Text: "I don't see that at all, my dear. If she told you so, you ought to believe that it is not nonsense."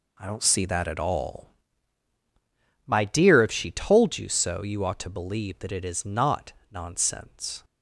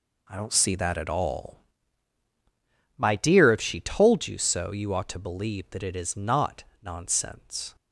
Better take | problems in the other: neither | pauses between "not" and "nonsense"; slight; the same in both

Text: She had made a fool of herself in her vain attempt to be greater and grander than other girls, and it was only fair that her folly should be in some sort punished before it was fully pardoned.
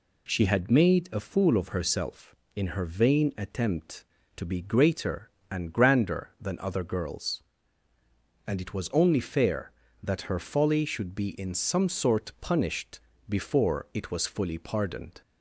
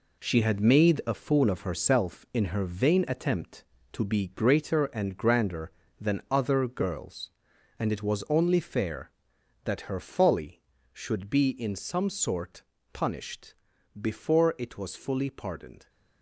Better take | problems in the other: first | gets quieter; strong; throughout; 8 dB // pauses between "sort" and "punished"; slight; at 12.6 s; 0.30 s long // pauses between "punished" and "before"; noticeable; at 13.5 s; 0.46 s long; slight in the first

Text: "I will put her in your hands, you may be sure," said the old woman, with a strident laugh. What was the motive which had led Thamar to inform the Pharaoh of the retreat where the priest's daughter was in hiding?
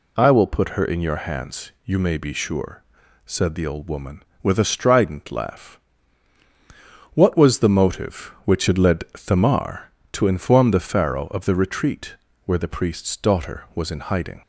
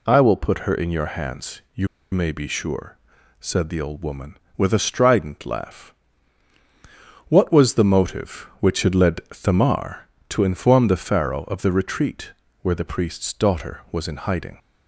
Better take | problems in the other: first | pauses between "you" and "may"; slight; at 1.8 s; 0.24 s long // pauses between "retreat" and "where"; slight; at 12.3 s; 0.30 s long; slight in the first

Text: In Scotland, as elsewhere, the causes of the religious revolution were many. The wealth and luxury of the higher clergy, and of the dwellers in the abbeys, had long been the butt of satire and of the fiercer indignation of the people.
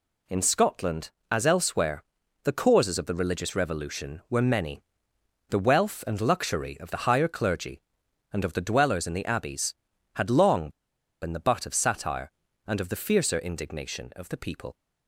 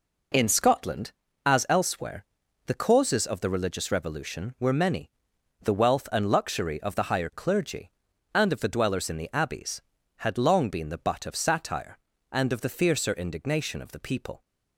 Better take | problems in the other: second | pauses between "long" and "been"; noticeable; at 10.6 s; 0.52 s long

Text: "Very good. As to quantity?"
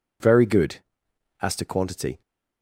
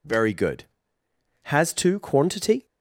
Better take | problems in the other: first | says "Has" for "As"; at 1.4 s

